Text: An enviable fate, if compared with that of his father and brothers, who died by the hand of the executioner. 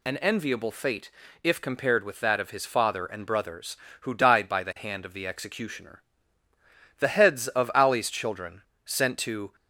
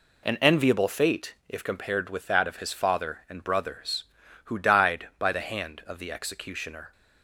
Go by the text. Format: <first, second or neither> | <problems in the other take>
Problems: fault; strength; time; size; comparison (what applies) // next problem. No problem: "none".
second | goes on to say "The heads of Ali's children sent to"; strong; from 6.9 s on; 2.5 s long